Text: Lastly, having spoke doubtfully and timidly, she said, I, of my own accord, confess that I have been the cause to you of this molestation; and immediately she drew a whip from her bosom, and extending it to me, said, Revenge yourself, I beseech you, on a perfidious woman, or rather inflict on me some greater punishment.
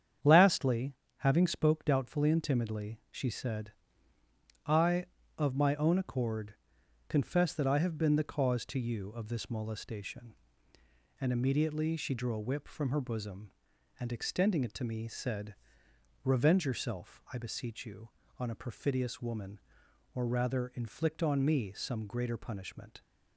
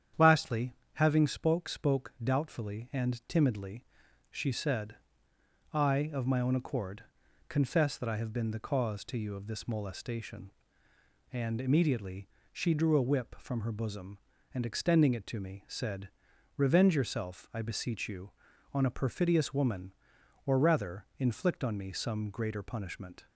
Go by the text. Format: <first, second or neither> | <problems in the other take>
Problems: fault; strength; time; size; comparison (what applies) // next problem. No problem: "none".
first | starts louder than the rest; strong; until 1.3 s; 9 dB; strong in the first // says "spoke" twice; at 1.6 s // pauses between "immediately" and "she"; slight; at 12.2 s; 0.22 s long